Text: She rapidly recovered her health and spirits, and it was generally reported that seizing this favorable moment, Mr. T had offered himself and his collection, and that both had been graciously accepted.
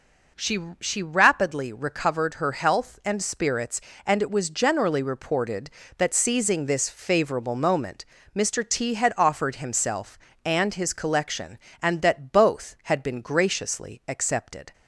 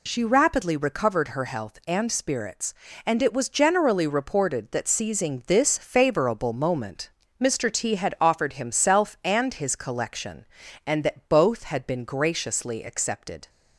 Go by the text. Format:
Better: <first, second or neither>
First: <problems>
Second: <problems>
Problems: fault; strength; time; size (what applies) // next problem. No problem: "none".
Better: second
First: says "She" twice; at 0.8 s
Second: none